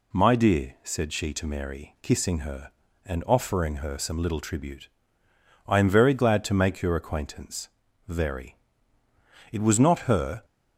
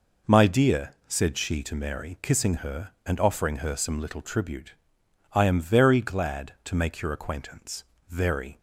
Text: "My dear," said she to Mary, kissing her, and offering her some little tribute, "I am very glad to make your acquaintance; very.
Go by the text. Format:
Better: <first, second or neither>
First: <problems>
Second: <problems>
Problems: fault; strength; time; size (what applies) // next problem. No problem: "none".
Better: second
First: goes on to say "It was not her"; noticeable; from 9.5 s on; 0.94 s long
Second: none